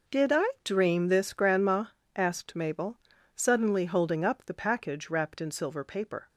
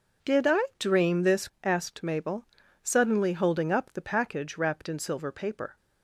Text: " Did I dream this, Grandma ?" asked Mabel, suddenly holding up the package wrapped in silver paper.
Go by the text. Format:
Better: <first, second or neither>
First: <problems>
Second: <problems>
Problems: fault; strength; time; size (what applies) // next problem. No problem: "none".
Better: first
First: none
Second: skips "Grandma"; at 1.4 s